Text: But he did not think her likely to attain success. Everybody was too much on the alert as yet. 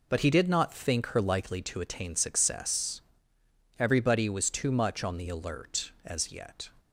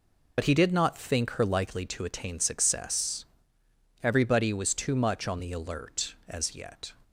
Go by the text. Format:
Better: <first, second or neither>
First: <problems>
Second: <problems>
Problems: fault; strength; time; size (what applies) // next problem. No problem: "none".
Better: first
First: none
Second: loses the start of "But"; at 0.3 s; 45 ms